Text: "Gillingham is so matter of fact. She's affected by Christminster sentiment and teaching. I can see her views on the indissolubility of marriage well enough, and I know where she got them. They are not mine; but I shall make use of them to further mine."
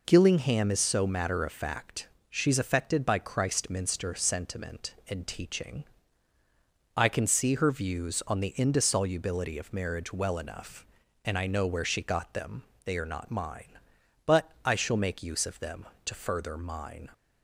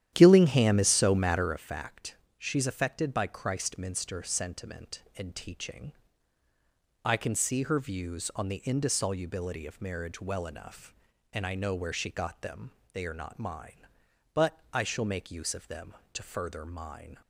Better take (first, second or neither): first